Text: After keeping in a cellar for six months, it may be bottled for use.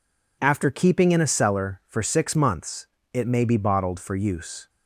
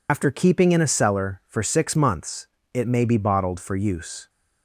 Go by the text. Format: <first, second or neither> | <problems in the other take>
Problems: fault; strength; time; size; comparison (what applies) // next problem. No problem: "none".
first | loses the start of "After"; at 0.0 s; 85 ms